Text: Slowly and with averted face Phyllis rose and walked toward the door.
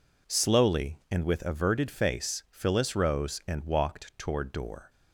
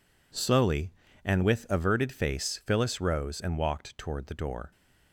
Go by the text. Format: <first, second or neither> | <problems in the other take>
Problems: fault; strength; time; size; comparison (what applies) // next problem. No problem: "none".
second | skips "the"; at 4.5 s